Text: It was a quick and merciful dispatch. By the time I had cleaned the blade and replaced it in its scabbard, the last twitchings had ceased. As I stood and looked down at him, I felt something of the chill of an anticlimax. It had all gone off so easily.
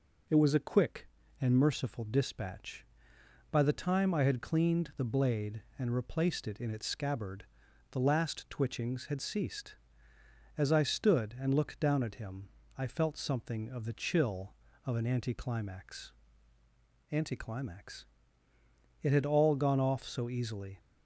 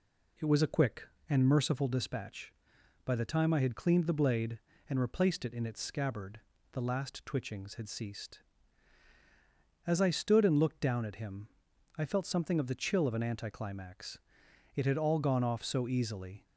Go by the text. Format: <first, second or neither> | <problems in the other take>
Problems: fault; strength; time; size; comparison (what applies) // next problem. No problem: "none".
second | says "anticlimax" twice; at 17.1 s